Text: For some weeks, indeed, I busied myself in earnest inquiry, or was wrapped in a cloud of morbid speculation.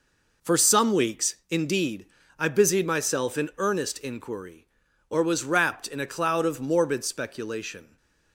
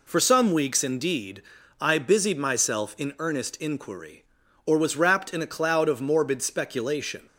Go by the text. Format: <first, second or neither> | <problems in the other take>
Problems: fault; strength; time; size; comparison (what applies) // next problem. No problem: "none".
neither | none